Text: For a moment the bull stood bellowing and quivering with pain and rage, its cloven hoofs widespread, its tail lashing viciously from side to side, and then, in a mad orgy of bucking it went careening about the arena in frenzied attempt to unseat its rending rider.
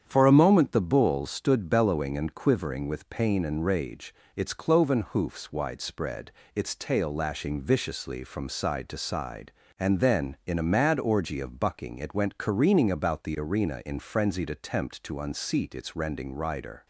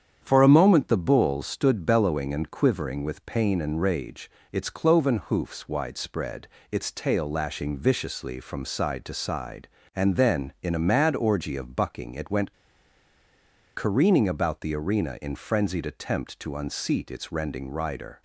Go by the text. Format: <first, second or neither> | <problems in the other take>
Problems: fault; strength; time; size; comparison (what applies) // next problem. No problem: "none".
first | starts louder than the rest; strong; until 1.2 s; 8.5 dB; strong in the first // pauses between "went" and "careening"; at 12.5 s; 1.2 s long